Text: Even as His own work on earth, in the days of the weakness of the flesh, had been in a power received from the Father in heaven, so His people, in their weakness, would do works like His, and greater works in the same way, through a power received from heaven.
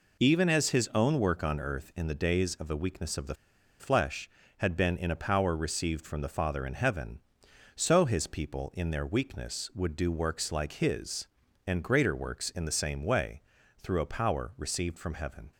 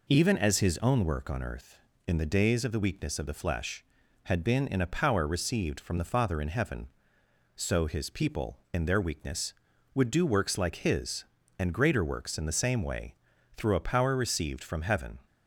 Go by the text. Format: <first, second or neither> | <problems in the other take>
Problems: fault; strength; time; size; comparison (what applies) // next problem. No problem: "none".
second | pauses between "the" and "flesh"; at 3.3 s; 0.44 s long